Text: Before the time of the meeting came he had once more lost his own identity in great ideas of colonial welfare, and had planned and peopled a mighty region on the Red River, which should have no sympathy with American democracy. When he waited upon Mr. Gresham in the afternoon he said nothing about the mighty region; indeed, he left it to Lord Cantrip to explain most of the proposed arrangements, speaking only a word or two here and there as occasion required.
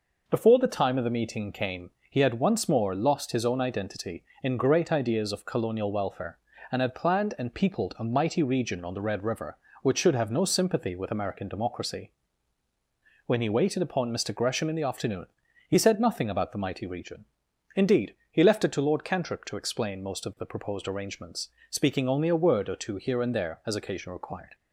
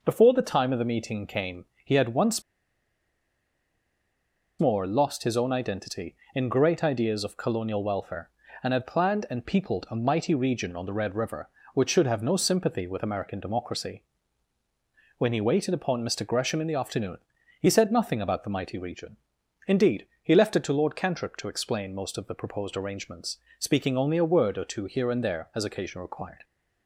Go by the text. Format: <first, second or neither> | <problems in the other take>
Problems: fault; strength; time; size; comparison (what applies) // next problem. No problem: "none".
first | pauses between "came" and "he"; slight; at 1.6 s; 0.18 s long; slight in the first // pauses between "once" and "more"; strong; at 2.4 s; 2.1 s long // pauses between "afternoon" and "he"; at 17.1 s; 0.40 s long; also in the first